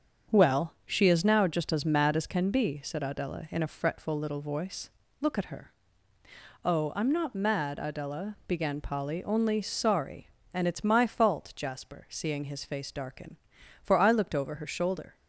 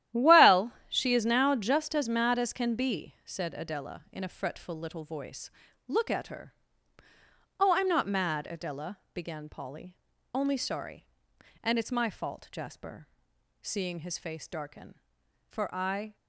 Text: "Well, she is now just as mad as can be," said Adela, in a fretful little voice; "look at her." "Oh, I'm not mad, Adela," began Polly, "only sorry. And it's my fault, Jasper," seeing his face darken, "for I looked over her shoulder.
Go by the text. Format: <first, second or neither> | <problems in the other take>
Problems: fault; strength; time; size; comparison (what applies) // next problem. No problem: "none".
first | starts louder than the rest; strong; until 1.3 s; 12 dB; strong in the first // stops before "looked over her shoulder"; at 16.1 s